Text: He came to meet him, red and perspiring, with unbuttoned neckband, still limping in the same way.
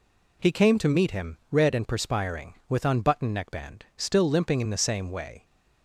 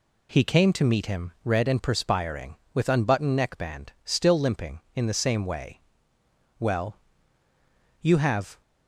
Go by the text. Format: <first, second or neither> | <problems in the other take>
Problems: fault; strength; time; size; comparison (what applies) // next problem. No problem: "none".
first | goes on to say "Well You have"; strong; from 6.6 s on; 2.0 s long